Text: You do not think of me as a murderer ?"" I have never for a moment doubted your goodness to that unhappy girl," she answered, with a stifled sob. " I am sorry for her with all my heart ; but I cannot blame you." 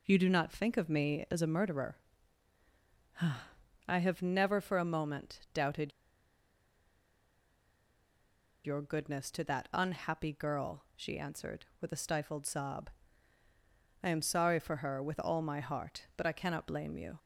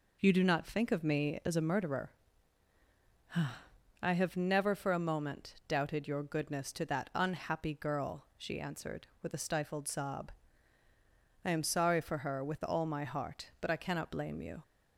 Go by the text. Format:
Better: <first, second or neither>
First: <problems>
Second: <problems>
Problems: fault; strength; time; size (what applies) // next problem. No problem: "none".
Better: second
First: pauses between "moment" and "doubted"; slight; at 5.3 s; 0.16 s long // pauses between "doubted" and "your"; strong; at 5.9 s; 2.7 s long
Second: pauses between "moment" and "doubted"; slight; at 5.5 s; 0.16 s long